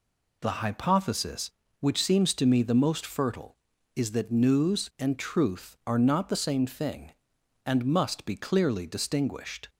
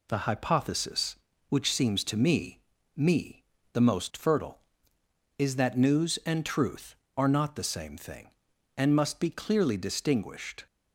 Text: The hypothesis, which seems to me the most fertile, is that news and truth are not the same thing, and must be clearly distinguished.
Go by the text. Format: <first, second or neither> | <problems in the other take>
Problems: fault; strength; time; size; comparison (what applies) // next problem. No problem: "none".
first | says "me" twice; at 2.9 s